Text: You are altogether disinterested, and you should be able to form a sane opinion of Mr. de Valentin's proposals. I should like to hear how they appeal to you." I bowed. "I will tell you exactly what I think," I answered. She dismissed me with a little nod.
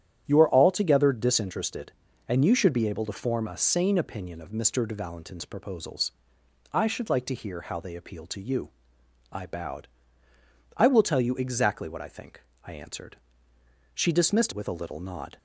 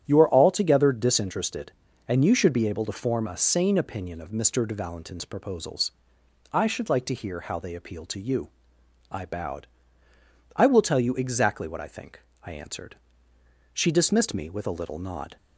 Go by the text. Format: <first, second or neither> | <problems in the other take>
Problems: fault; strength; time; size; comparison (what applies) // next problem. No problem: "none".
second | starts louder than the rest; strong; until 1.2 s; 10 dB; strong in the second // skips "me"; at 14.5 s